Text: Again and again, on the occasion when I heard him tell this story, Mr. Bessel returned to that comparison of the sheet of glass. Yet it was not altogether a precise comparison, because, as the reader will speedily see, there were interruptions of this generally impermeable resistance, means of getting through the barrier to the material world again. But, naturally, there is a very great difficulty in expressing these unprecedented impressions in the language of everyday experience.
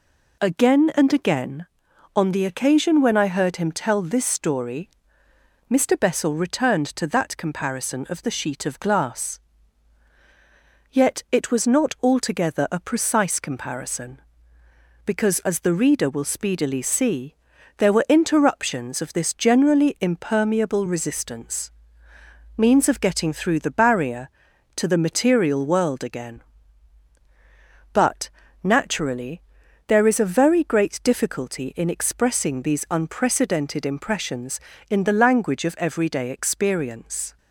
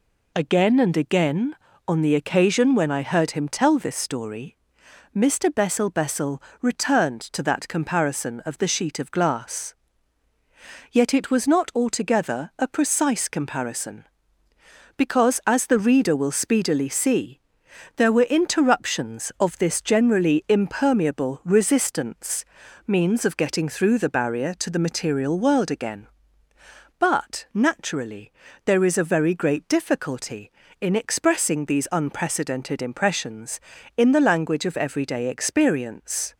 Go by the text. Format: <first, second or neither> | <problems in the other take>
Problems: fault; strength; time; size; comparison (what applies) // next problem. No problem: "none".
first | says "Bessel" twice; at 5.8 s